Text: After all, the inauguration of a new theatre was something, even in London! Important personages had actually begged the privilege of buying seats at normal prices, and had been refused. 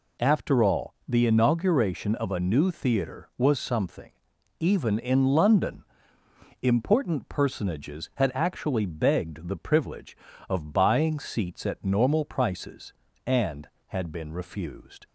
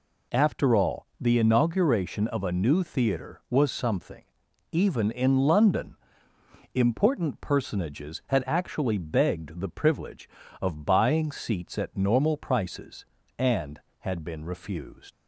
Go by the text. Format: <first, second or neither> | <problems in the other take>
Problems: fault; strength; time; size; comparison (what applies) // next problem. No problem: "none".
first | leaves "refused" unfinished; at 15.1 s; 50 ms